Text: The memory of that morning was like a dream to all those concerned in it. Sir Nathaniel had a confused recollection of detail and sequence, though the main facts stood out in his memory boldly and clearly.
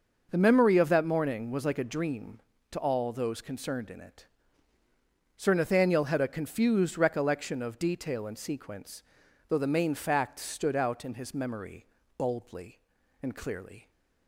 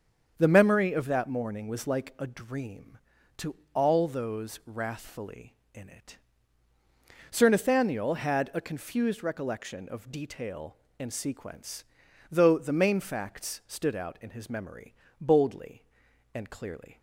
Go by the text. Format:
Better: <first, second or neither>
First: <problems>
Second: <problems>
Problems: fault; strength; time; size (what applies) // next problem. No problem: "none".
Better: first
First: pauses between "memory" and "boldly"; slight; at 11.8 s; 0.30 s long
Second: starts louder than the rest; strong; until 1.3 s; 7 dB // pauses between "to" and "all"; slight; at 3.5 s; 0.18 s long // says "wrathfully" for "concerned"; at 4.6 s // pauses between "memory" and "boldly"; slight; at 14.9 s; 0.28 s long